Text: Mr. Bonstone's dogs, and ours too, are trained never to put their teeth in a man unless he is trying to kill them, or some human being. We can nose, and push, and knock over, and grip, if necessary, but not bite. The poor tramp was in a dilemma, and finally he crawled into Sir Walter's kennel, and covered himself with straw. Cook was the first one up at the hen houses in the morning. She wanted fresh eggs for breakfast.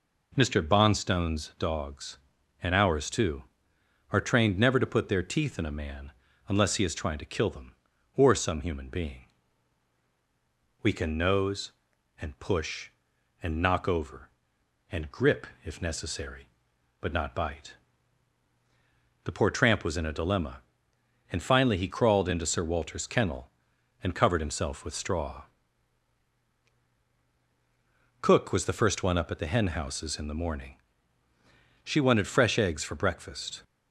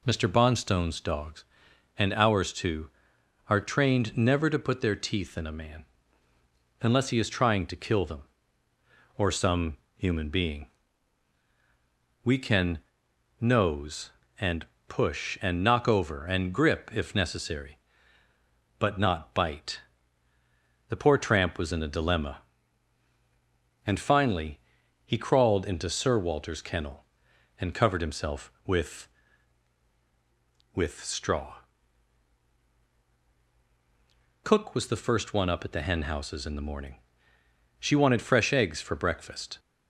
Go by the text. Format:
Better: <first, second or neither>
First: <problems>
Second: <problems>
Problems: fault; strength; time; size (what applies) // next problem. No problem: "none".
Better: first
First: pauses between "man" and "unless"; at 6.1 s; 0.38 s long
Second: pauses between "man" and "unless"; noticeable; at 5.8 s; 0.96 s long // pauses between "some" and "human"; slight; at 9.7 s; 0.18 s long // pauses between "can" and "nose"; noticeable; at 12.7 s; 0.60 s long // pauses between "and" and "push"; slight; at 14.6 s; 0.24 s long // pauses between "finally" and "he"; noticeable; at 24.5 s; 0.46 s long // says "with" twice; at 30.7 s